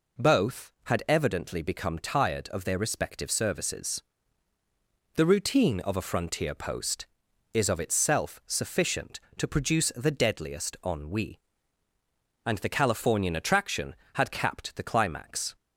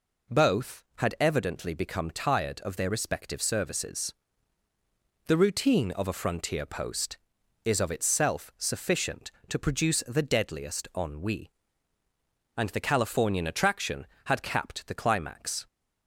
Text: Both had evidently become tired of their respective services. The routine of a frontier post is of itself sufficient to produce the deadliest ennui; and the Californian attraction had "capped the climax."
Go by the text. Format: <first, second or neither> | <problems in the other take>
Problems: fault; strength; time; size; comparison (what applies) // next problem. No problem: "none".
neither | none